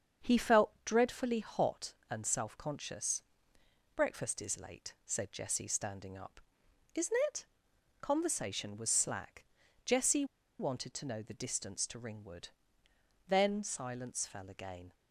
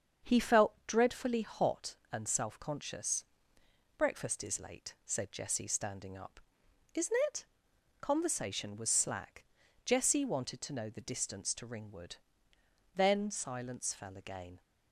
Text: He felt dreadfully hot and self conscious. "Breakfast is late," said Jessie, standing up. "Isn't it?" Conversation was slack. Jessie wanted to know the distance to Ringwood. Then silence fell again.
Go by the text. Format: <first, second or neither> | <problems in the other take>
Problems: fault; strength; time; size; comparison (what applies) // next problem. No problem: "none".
second | starts louder than the rest; strong; until 1.3 s; 7.5 dB; strong in the second // pauses between "Jessie" and "wanted"; slight; at 10.2 s; 0.35 s long